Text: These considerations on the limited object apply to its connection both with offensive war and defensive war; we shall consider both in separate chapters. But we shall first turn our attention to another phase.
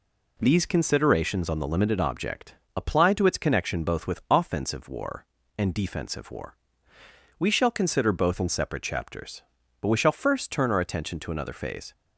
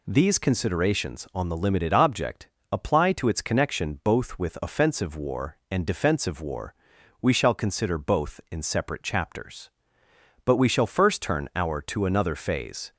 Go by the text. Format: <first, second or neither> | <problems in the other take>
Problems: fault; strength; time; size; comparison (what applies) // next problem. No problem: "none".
first | pauses between "object" and "apply"; slight; at 2.4 s; 0.24 s long; slight in the first // skips "attention"; at 11.8 s